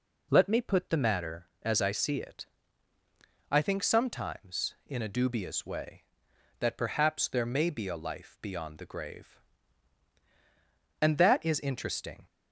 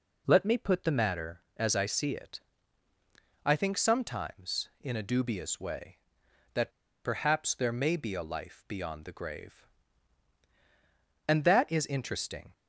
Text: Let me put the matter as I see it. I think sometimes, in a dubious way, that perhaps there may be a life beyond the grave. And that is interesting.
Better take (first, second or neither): first